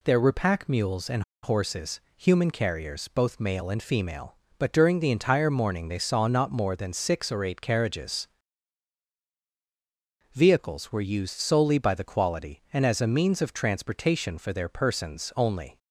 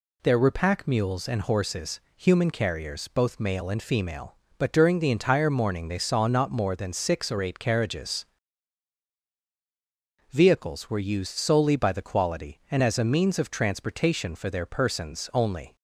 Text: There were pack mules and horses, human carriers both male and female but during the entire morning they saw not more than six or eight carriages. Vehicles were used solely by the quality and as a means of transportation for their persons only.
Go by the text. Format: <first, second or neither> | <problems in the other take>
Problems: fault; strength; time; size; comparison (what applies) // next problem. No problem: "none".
second | pauses between "and" and "horses"; slight; at 1.2 s; 0.21 s long